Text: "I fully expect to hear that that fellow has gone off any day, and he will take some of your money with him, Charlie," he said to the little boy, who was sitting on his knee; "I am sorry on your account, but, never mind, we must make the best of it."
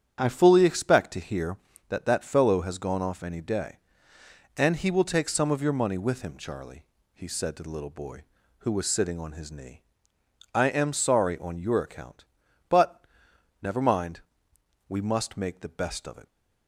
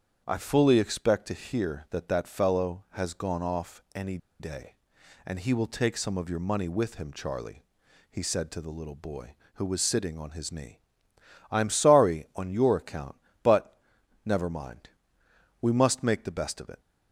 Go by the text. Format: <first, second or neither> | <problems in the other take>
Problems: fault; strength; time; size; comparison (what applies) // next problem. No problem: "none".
first | starts louder than the rest; strong; until 1.2 s; 8 dB; strong in the first // pauses between "any" and "day"; slight; at 4.1 s; 0.22 s long